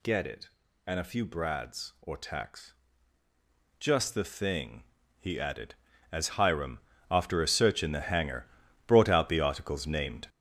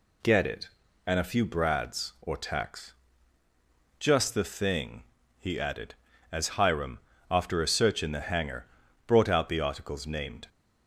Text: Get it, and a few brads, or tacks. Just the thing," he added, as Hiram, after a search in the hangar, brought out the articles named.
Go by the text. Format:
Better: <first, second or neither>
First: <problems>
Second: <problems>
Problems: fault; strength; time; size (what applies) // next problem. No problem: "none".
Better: second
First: gets louder; strong; throughout; 7.5 dB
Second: none